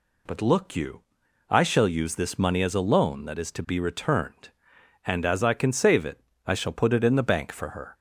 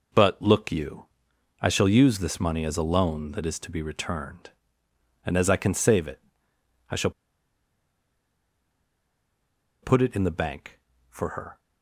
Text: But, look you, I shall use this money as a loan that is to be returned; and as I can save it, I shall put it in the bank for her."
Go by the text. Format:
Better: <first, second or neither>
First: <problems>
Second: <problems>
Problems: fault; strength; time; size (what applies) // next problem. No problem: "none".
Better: first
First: none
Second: pauses between "shall" and "put"; strong; at 7.0 s; 2.7 s long